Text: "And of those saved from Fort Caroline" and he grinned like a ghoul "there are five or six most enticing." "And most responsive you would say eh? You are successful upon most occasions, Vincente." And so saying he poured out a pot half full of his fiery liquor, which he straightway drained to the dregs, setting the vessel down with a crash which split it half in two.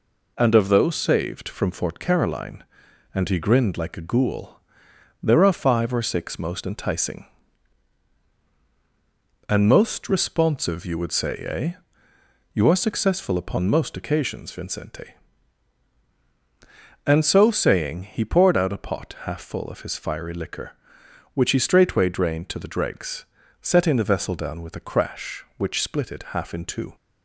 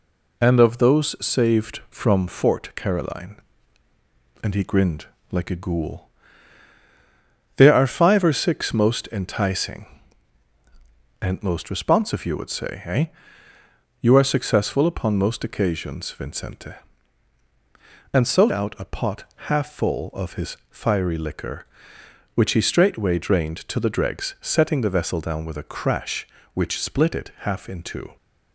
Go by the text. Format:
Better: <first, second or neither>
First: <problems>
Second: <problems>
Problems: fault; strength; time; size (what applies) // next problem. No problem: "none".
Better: first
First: pauses between "ghoul" and "there"; noticeable; at 4.5 s; 0.64 s long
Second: pauses between "grinned" and "like"; slight; at 5.0 s; 0.26 s long // pauses between "ghoul" and "there"; strong; at 6.0 s; 1.4 s long // skips "saying he poured"; at 18.4 s // pauses between "pot" and "half"; slight; at 19.2 s; 0.26 s long